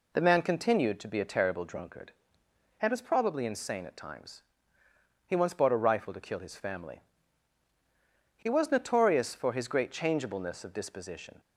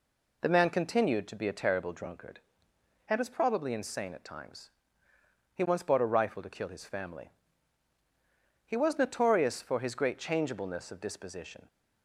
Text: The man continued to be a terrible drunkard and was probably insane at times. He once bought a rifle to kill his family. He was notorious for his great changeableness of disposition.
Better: neither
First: none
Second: none

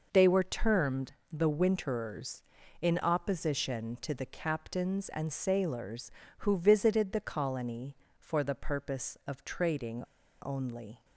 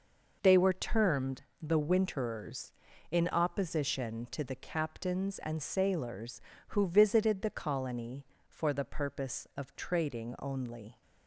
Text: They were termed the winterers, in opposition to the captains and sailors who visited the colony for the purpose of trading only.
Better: second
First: pauses between "termed" and "the"; slight; at 1.1 s; 0.20 s long // pauses between "trading" and "only"; at 10.0 s; 0.41 s long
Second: pauses between "termed" and "the"; slight; at 1.4 s; 0.20 s long

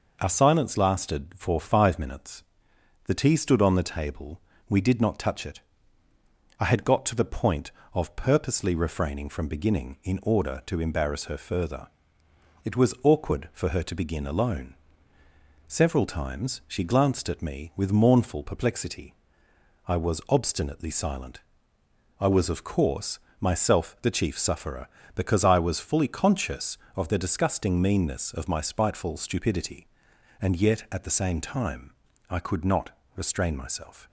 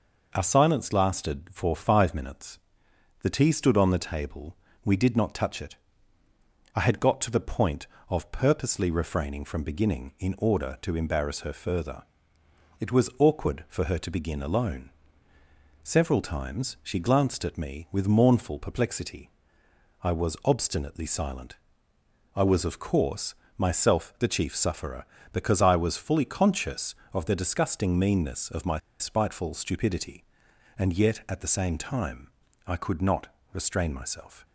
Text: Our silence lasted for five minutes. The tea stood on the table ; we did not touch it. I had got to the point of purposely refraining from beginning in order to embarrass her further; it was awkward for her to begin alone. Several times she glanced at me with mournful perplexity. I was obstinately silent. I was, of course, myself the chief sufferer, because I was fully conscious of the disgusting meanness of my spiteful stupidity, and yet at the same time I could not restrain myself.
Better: first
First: pauses between "time" and "I"; at 31.9 s; 0.38 s long // pauses between "not" and "restrain"; slight; at 32.8 s; 0.26 s long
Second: pauses between "my" and "spiteful"; slight; at 28.7 s; 0.20 s long // pauses between "time" and "I"; at 32.2 s; 0.38 s long // pauses between "not" and "restrain"; slight; at 33.2 s; 0.26 s long

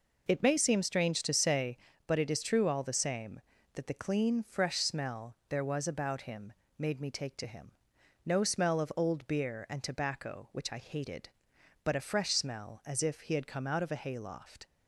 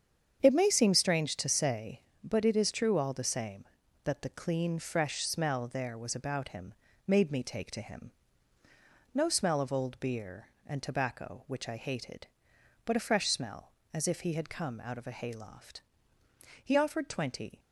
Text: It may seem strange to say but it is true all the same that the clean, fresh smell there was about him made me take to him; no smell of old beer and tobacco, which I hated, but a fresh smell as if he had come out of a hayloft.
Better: first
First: pauses between "him" and "made"; slight; at 6.5 s; 0.26 s long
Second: starts louder than the rest; strong; until 1.4 s; 8 dB // pauses between "him" and "made"; slight; at 6.7 s; 0.32 s long // goes on to say "He offered twenty"; noticeable; from 16.6 s on; 0.94 s long

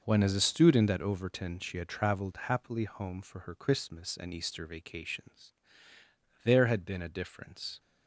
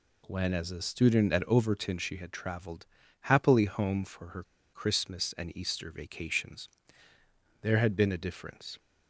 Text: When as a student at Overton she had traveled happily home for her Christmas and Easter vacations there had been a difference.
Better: first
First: pauses between "vacations" and "there"; noticeable; at 5.5 s; 0.92 s long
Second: pauses between "traveled" and "happily"; slight; at 2.8 s; 0.34 s long // pauses between "her" and "Christmas"; slight; at 4.4 s; 0.30 s long // pauses between "vacations" and "there"; noticeable; at 6.6 s; 0.94 s long

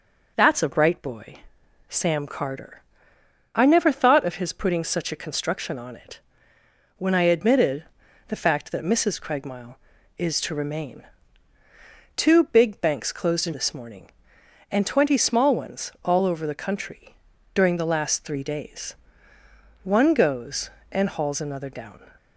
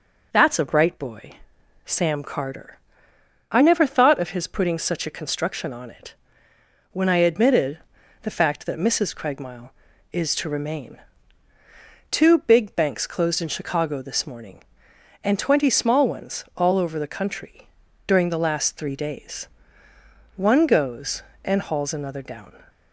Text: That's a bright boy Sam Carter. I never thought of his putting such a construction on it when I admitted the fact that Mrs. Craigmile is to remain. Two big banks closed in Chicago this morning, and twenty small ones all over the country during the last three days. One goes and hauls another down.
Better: second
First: pauses between "boy" and "Sam"; noticeable; at 1.3 s; 0.52 s long // pauses between "it" and "when"; noticeable; at 6.1 s; 0.80 s long // pauses between "admitted" and "the"; at 7.8 s; 0.44 s long // skips "Chicago"; at 13.5 s // pauses between "country" and "during"; at 17.1 s; 0.38 s long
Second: pauses between "boy" and "Sam"; noticeable; at 1.3 s; 0.52 s long // pauses between "it" and "when"; noticeable; at 6.1 s; 0.80 s long // pauses between "admitted" and "the"; at 7.7 s; 0.44 s long // pauses between "country" and "during"; at 17.6 s; 0.38 s long

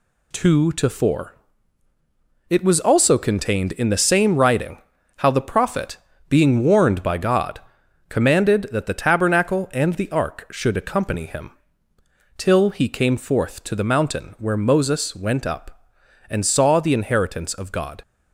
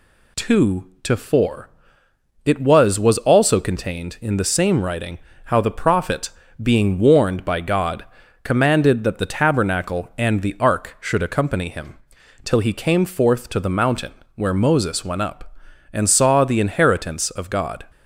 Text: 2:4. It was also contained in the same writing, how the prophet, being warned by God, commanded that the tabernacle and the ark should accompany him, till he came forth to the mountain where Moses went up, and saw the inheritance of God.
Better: first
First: none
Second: says "was" twice; at 2.9 s // pauses between "mountain" and "where"; slight; at 14.1 s; 0.22 s long

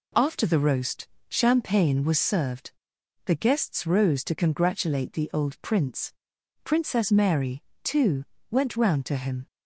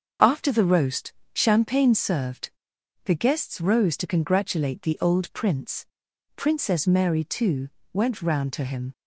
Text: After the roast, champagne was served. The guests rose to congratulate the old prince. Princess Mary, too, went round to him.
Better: first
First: none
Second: skips "was"; at 1.9 s

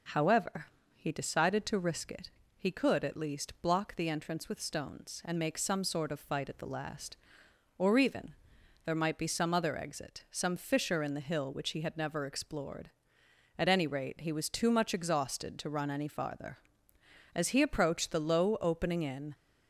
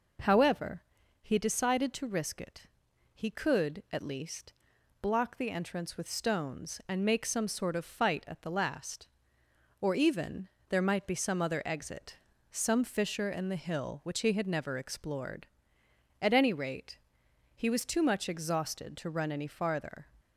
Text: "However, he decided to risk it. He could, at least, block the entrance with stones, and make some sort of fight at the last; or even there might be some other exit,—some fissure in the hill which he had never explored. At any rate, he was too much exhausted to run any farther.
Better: second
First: pauses between "even" and "there"; noticeable; at 8.3 s; 0.52 s long // goes on to say "As he approached the low opening in"; strong; from 17.3 s on; 2.0 s long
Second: pauses between "even" and "there"; slight; at 10.5 s; 0.18 s long

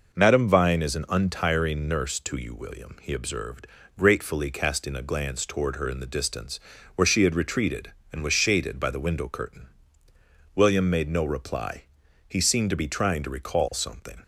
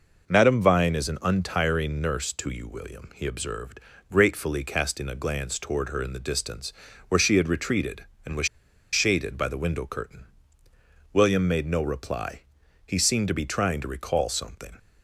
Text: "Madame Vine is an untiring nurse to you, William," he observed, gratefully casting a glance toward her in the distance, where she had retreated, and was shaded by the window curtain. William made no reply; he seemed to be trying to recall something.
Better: first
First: none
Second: pauses between "was" and "shaded"; at 8.4 s; 0.45 s long

